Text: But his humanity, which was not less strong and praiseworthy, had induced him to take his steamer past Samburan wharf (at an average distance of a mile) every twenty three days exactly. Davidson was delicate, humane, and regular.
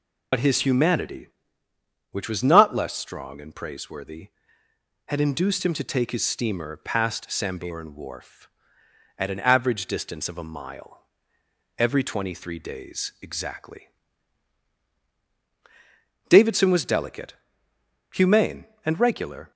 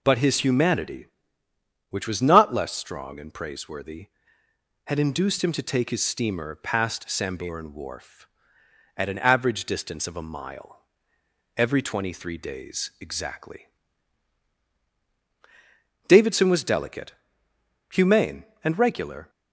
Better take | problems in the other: second | loses the start of "But"; at 0.3 s; 75 ms

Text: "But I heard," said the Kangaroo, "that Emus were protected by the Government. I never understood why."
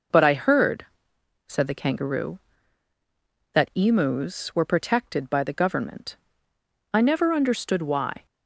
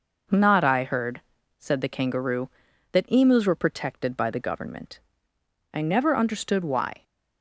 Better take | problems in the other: first | says "Not" for "But"; at 0.2 s

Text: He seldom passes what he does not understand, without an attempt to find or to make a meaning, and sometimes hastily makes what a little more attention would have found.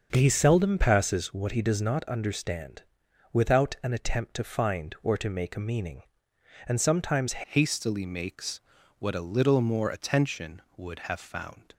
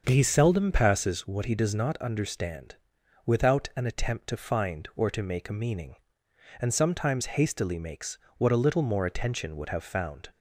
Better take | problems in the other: second | starts louder than the rest; until 1.1 s; 6.5 dB; also in the second // changes voice at "hastily"; from 7.4 s on; 4.3 s long // pauses between "makes" and "what"; at 8.6 s; 0.38 s long; slight in the second

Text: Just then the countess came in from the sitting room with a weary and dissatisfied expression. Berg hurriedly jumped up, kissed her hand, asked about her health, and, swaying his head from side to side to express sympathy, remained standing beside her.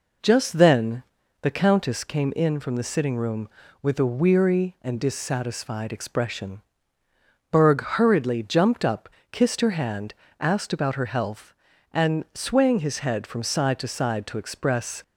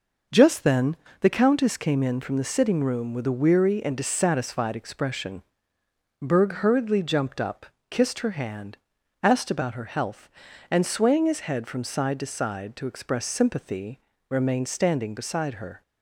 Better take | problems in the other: second | pauses between "then" and "the"; at 1.0 s; 0.38 s long; slight in the second // stops before "sympathy remained standing beside her"; at 15.0 s

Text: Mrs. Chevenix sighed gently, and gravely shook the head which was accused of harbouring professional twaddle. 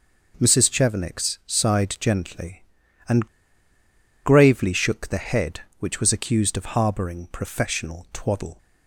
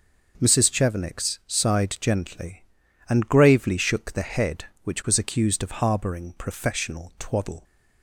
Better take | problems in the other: second | pauses between "and" and "gravely"; noticeable; at 3.2 s; 0.96 s long

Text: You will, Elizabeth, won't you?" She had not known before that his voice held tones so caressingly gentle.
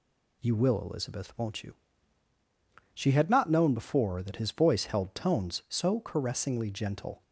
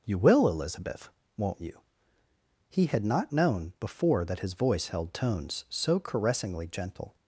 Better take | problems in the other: first | says "He" for "She"; at 2.6 s

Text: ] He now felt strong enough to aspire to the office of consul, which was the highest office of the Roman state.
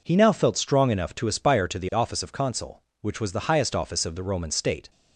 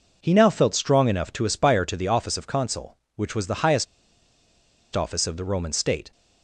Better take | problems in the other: first | pauses between "highest" and "office"; at 3.8 s; 1.0 s long

